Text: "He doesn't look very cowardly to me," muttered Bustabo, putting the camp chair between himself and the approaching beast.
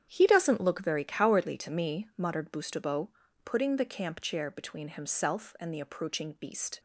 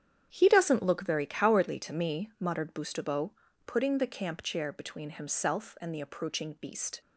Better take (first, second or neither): neither